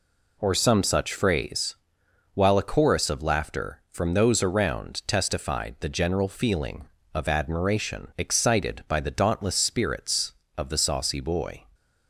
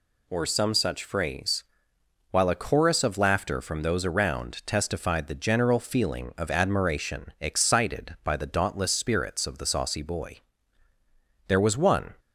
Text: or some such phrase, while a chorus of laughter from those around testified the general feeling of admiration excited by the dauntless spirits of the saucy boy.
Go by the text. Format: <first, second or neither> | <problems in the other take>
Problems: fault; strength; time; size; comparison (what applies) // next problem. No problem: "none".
first | goes on to say "There was one"; noticeable; from 11.4 s on; 0.68 s long